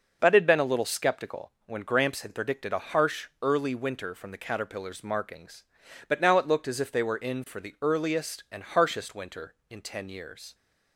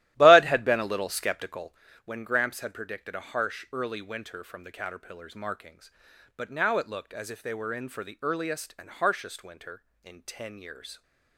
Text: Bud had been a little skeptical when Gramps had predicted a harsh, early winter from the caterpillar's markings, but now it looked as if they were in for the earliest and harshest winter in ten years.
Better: first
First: none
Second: starts louder than the rest; strong; until 1.9 s; 14 dB // pauses between "skeptical" and "when"; slight; at 1.7 s; 0.30 s long

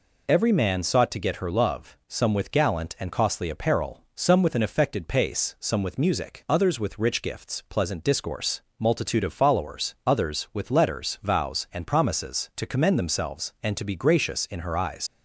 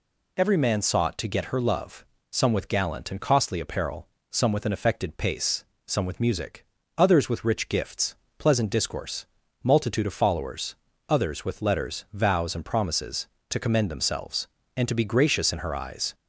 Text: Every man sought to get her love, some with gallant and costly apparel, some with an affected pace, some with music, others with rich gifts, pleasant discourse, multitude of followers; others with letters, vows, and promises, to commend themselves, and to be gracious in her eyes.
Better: second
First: leaves "eyes" unfinished; at 15.0 s; 65 ms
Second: none

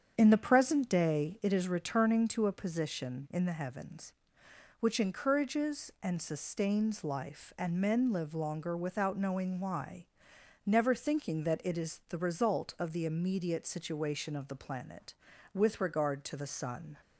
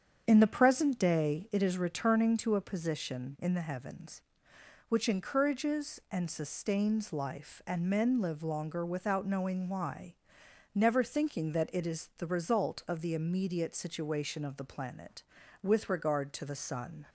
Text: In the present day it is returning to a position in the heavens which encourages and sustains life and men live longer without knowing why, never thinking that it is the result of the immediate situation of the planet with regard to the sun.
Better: neither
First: starts louder than the rest; strong; until 1.1 s; 7.5 dB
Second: starts louder than the rest; strong; until 1.2 s; 7.5 dB

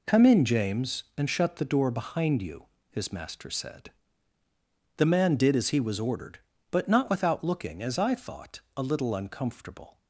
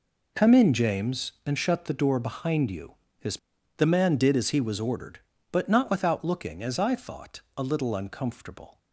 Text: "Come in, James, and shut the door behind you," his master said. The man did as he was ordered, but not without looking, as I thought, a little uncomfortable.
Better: first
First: none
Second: skips "master said"; at 3.5 s

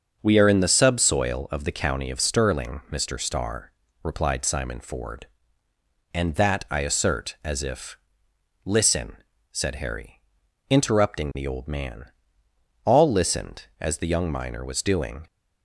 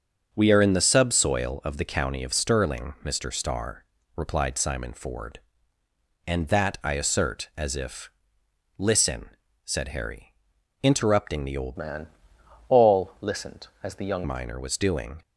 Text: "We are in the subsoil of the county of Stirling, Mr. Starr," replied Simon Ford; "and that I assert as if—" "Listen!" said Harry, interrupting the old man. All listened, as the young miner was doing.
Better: first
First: starts louder than the rest; until 1.2 s; 6.5 dB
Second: starts louder than the rest; until 1.3 s; 6.5 dB // changes voice from "man" to "young"; from 11.7 to 14.2 s; 2.5 s long

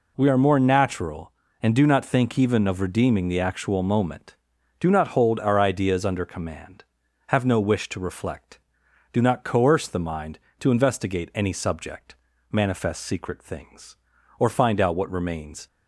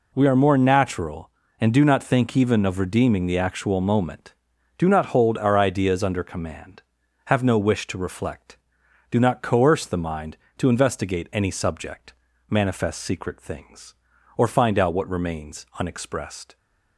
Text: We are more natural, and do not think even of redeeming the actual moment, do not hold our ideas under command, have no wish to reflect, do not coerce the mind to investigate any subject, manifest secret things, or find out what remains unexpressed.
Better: second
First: stops before "unexpressed"; at 15.6 s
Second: none

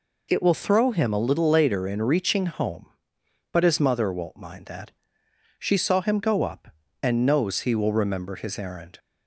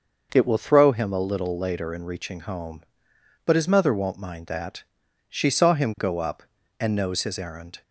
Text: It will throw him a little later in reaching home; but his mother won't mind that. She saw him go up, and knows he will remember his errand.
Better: first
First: none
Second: starts louder than the rest; noticeable; until 1.3 s; 6 dB // skips "he will remember"; at 7.2 s

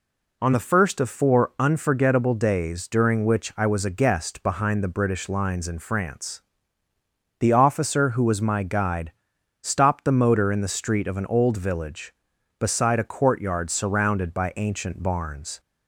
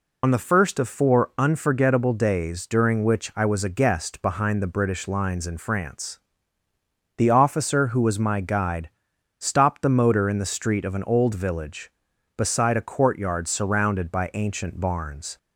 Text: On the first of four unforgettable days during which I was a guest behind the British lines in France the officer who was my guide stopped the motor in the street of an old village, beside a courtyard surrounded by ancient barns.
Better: first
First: pauses between "France" and "the"; noticeable; at 6.4 s; 0.96 s long // pauses between "guide" and "stopped"; noticeable; at 9.1 s; 0.50 s long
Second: loses the start of "On"; at 0.2 s; 65 ms // pauses between "France" and "the"; noticeable; at 6.1 s; 0.96 s long // pauses between "guide" and "stopped"; noticeable; at 8.8 s; 0.50 s long

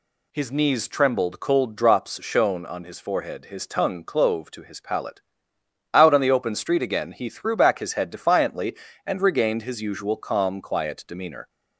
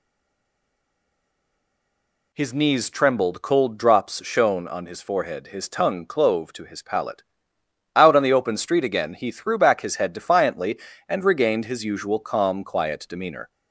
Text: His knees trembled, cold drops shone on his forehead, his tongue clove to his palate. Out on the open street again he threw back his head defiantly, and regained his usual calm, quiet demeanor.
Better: first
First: none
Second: stays silent before the first word; until 2.3 s; 2.3 s long

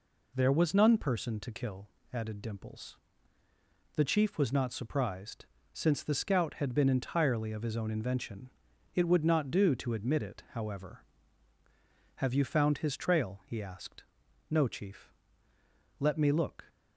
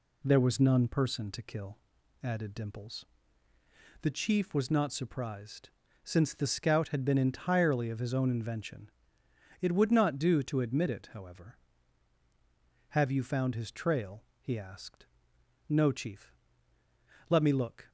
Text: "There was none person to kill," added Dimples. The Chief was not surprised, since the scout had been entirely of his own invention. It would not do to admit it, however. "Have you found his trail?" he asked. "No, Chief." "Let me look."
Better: neither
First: none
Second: none

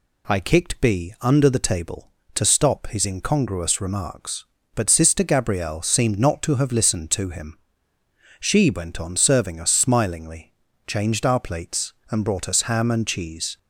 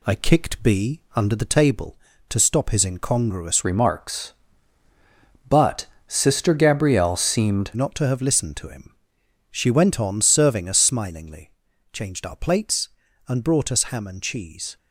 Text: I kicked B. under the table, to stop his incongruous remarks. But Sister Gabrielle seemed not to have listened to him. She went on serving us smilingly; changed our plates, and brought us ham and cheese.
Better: first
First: none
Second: changes voice from "remarks" to "seemed"; from 3.6 to 7.7 s; 4.1 s long // pauses between "But" and "Sister"; slight; at 5.8 s; 0.24 s long

